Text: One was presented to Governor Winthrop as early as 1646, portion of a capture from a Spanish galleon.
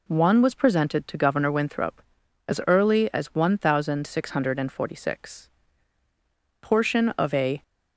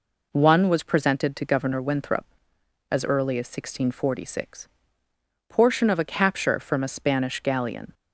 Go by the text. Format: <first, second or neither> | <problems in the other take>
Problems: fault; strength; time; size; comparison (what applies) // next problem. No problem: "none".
second | stops before "capture from a Spanish galleon"; at 7.6 s